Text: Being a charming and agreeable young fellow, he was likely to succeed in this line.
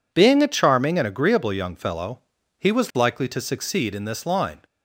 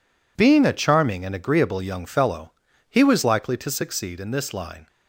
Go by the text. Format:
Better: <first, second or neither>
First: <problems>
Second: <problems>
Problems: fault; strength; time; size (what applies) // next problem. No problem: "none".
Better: neither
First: none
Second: none